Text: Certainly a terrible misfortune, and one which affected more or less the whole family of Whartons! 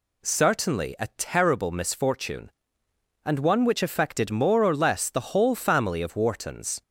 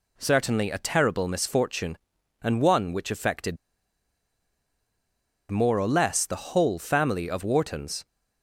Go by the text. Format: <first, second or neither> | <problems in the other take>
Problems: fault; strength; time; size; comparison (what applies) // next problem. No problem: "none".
first | pauses between "affected" and "more"; strong; at 3.5 s; 1.9 s long